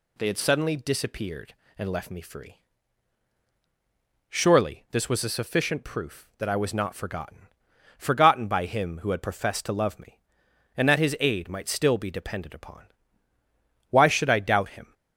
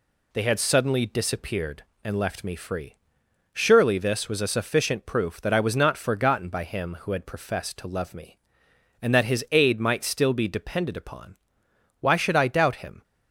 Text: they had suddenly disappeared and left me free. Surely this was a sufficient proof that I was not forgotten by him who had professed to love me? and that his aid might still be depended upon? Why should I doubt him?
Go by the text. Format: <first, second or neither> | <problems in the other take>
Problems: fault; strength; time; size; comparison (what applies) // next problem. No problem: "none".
second | says "forgotten" twice; at 7.9 s